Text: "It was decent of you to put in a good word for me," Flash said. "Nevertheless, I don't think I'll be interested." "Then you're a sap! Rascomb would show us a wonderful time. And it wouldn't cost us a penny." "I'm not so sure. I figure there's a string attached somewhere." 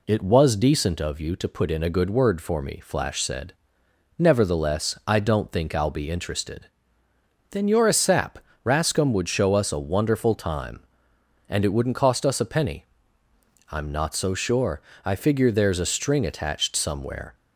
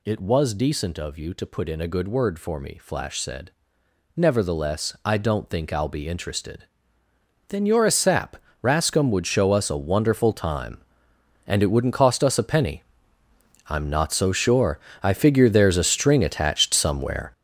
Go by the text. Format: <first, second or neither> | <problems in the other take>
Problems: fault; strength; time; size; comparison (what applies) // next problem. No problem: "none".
first | gets louder; strong; throughout; 9.5 dB